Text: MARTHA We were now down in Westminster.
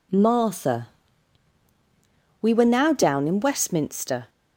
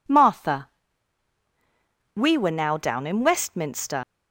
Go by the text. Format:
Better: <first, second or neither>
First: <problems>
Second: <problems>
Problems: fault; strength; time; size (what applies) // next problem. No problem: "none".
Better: first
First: pauses between "MARTHA" and "We"; strong; at 0.8 s; 1.5 s long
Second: pauses between "MARTHA" and "We"; strong; at 0.6 s; 1.4 s long // leaves "Westminster" unfinished; at 4.0 s; 90 ms